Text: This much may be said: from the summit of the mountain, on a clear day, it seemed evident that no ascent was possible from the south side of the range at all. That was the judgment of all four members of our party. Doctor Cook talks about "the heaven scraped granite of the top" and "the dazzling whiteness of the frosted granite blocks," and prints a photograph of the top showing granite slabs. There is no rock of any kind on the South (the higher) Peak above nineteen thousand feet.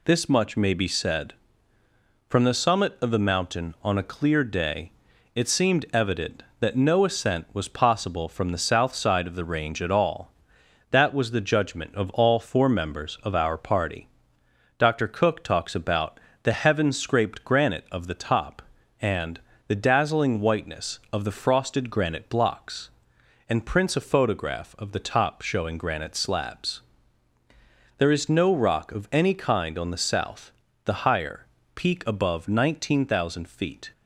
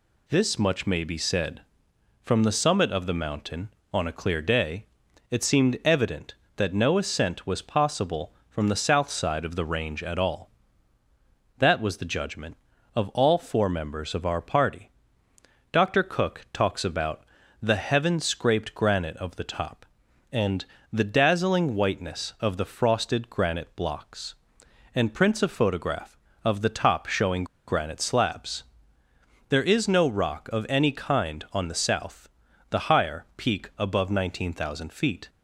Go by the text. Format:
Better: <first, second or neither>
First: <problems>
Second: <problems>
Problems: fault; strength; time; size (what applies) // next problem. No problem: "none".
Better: first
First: pauses between "about" and "the"; slight; at 16.1 s; 0.22 s long // pauses between "and" and "the"; slight; at 19.3 s; 0.28 s long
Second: pauses between "about" and "the"; at 17.2 s; 0.40 s long // pauses between "and" and "the"; slight; at 20.6 s; 0.26 s long // pauses between "showing" and "granite"; slight; at 27.4 s; 0.23 s long